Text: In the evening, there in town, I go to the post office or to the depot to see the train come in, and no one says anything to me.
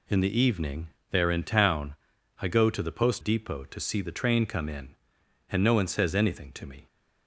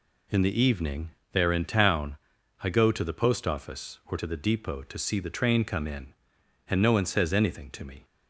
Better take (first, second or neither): second